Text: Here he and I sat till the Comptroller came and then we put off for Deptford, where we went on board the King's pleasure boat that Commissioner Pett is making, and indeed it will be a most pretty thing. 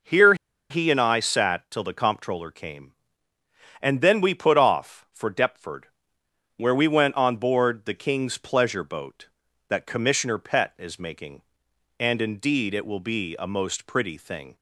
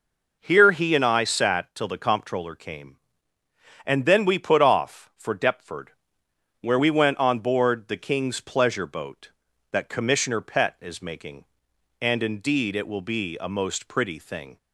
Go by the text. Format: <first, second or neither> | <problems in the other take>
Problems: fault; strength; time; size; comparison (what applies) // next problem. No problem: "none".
second | pauses between "Here" and "he"; slight; at 0.3 s; 0.36 s long